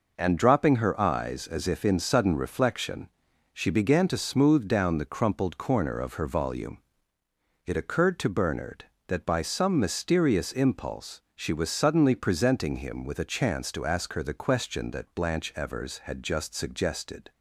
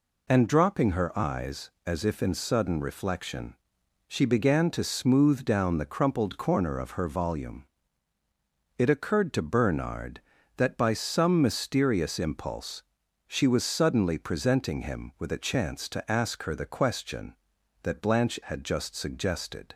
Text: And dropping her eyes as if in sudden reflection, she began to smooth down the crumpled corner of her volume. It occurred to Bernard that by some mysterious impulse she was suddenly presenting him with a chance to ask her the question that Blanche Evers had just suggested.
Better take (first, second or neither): first